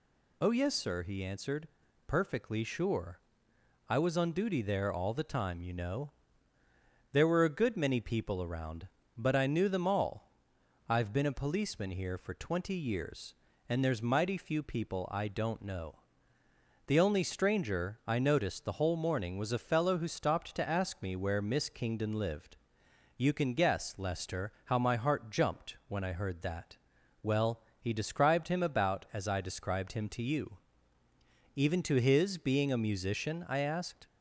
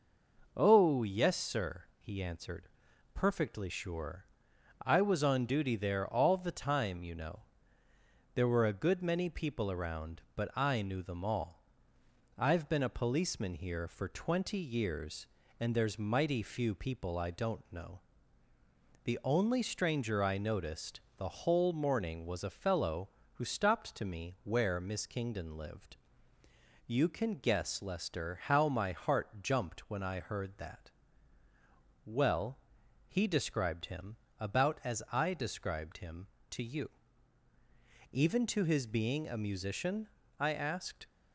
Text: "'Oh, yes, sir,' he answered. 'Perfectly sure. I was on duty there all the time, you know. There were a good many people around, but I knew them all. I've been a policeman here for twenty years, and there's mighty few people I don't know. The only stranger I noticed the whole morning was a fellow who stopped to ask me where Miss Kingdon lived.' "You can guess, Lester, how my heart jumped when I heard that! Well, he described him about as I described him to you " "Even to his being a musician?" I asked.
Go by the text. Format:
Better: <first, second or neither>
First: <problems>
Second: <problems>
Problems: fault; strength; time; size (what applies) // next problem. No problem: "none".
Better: first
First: none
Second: pauses between "noticed" and "the"; slight; at 21.0 s; 0.16 s long // skips "ask"; at 24.0 s // pauses between "him" and "about"; slight; at 34.1 s; 0.24 s long